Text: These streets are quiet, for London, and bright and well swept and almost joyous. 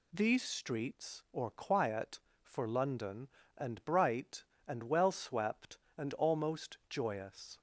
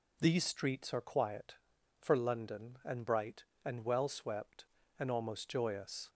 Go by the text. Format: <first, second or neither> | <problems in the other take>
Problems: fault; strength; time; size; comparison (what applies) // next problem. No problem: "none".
second | says "or" for "are"; at 1.3 s